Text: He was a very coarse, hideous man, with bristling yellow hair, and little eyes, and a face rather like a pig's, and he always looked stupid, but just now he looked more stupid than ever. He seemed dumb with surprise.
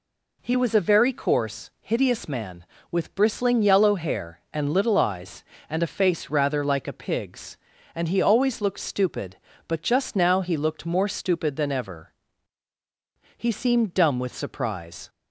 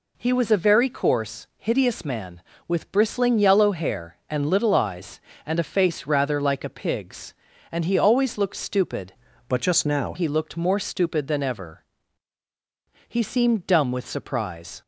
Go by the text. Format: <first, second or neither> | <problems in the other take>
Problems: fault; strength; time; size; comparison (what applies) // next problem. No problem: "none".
first | changes voice from "but" to "now"; from 9.4 to 10.1 s; 0.7 s long